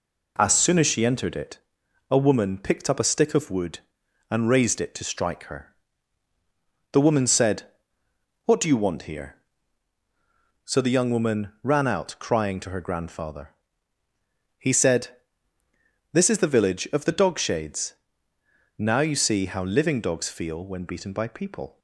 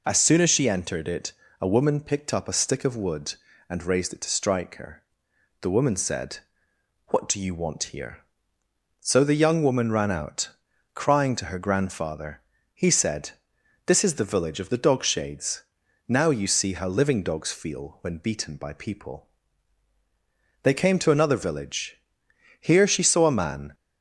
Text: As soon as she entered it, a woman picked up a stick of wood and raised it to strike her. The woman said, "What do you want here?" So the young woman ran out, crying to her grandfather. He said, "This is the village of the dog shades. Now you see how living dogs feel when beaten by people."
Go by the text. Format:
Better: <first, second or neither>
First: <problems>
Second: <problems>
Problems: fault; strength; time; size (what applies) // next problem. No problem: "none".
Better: first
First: none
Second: goes on to say "They came to another village Here she saw a man"; strong; from 20.6 s on; 3.1 s long